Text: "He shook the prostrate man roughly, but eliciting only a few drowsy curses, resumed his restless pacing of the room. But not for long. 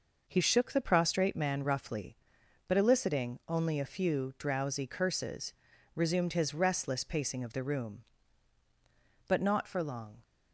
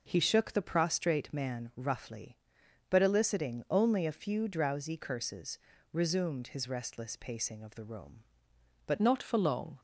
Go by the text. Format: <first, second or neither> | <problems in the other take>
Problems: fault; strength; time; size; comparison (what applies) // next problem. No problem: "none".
first | changes voice at "not"; from 8.9 s on; 0.8 s long